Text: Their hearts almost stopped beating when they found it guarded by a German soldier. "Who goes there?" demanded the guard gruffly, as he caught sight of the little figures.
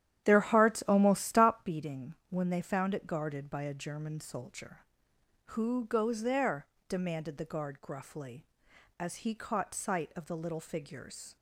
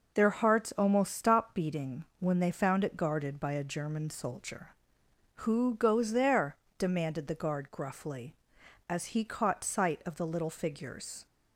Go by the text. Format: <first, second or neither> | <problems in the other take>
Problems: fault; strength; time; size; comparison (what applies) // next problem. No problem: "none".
second | starts louder than the rest; strong; until 1.7 s; 10.5 dB // pauses between "beating" and "when"; slight; at 2.1 s; 0.16 s long; slight in the second